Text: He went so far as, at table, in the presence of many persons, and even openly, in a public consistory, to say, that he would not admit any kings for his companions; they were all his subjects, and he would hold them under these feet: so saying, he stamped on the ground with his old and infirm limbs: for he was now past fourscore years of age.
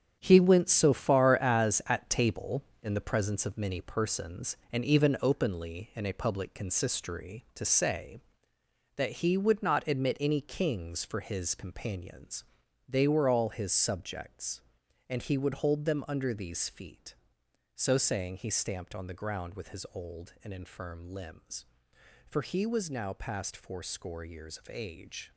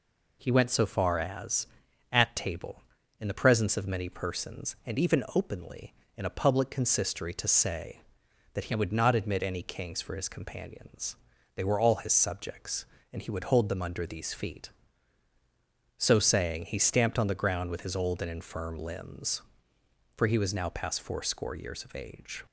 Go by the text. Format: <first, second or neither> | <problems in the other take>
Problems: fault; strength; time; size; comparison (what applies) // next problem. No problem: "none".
second | gets quieter; strong; throughout; 9.5 dB